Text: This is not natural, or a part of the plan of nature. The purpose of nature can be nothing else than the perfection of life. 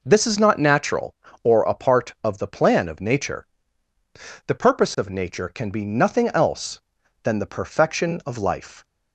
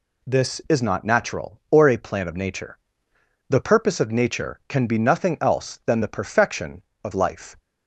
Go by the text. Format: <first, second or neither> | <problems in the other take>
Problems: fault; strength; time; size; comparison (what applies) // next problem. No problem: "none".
first | skips "part of the"; at 1.9 s